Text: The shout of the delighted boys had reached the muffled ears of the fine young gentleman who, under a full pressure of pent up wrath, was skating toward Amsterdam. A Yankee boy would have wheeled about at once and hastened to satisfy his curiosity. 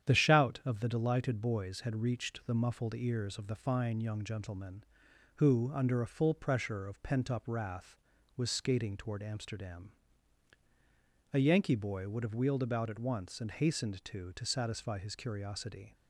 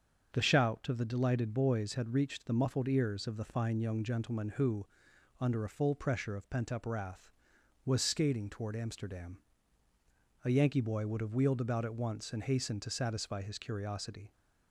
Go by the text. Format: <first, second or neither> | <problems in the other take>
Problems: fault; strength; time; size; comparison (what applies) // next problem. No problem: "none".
second | starts louder than the rest; strong; until 1.1 s; 9.5 dB; strong in the second // says "to" twice; at 14.3 s